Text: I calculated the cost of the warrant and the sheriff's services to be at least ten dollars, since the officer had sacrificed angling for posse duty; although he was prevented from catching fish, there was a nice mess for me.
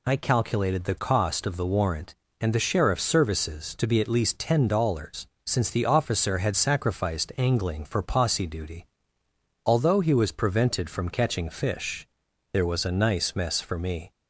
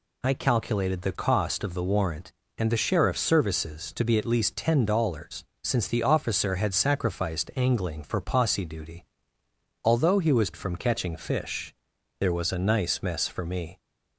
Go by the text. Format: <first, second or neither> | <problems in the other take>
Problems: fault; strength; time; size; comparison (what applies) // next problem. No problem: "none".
first | skips "prevented"; at 10.5 s